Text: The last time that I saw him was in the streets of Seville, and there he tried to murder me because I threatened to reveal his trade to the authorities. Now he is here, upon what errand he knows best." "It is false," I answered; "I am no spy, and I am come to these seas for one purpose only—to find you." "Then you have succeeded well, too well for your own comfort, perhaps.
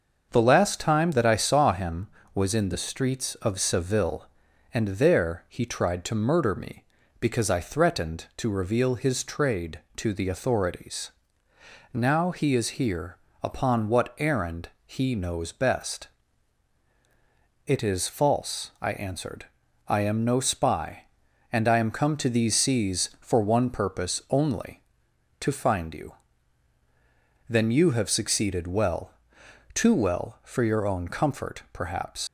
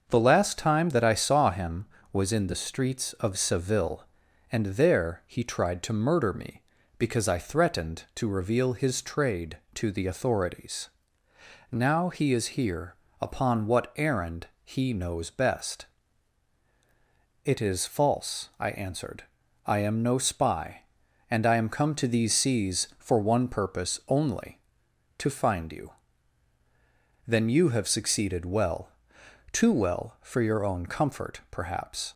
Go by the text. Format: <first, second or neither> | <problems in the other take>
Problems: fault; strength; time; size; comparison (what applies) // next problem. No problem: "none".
second | starts louder than the rest; until 1.3 s; 6.5 dB; also in the second // pauses between "errand" and "he"; slight; at 14.6 s; 0.16 s long; slight in the second // leaves "perhaps" unfinished; at 32.2 s; 75 ms